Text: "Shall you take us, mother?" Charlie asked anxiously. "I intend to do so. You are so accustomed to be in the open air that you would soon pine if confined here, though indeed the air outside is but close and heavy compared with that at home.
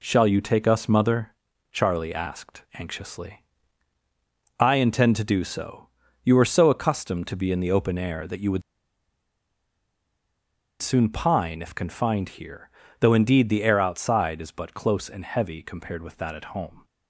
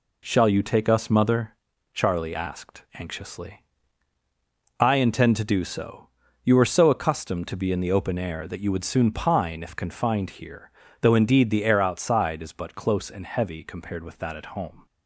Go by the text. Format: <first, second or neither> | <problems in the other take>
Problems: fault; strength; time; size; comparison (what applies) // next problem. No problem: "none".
second | pauses between "would" and "soon"; strong; at 8.6 s; 2.2 s long